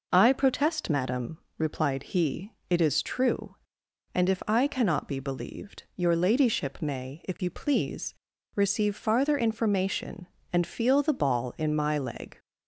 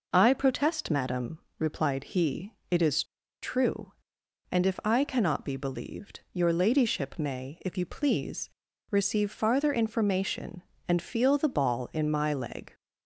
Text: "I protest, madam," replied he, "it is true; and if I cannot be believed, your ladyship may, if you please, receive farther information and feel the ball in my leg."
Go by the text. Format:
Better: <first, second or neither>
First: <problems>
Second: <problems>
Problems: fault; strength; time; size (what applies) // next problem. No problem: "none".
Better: first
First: none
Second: pauses between "is" and "true"; at 3.0 s; 0.39 s long